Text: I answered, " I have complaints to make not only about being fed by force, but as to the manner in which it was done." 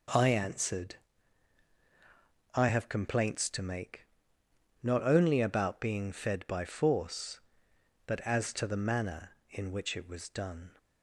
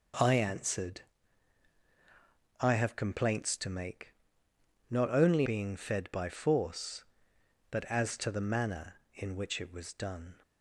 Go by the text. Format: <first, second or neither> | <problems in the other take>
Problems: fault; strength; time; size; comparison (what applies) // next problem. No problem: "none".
first | pauses between "make" and "not"; noticeable; at 4.1 s; 0.76 s long; noticeable in the first // skips "about"; at 5.4 s